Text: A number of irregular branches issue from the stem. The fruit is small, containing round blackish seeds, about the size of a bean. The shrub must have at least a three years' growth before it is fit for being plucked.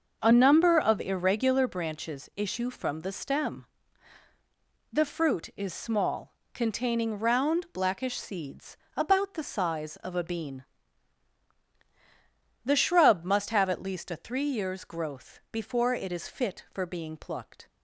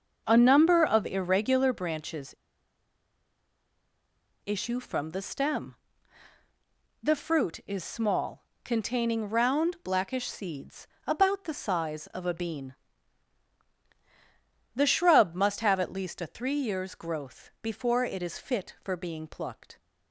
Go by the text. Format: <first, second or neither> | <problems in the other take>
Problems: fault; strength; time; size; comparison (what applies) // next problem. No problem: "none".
first | pauses between "branches" and "issue"; strong; at 2.3 s; 2.1 s long